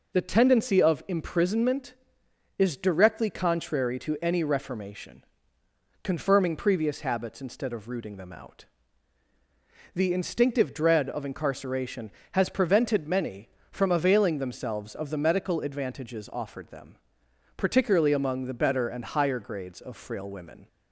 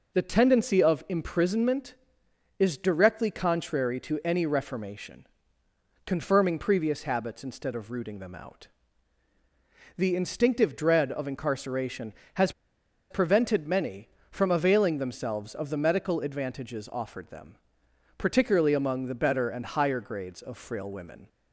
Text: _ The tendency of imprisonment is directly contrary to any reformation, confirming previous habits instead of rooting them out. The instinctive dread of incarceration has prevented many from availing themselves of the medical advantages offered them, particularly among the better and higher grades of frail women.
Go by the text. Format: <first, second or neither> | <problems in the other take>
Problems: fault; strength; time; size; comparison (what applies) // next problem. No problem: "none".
first | pauses between "has" and "prevented"; noticeable; at 12.5 s; 0.59 s long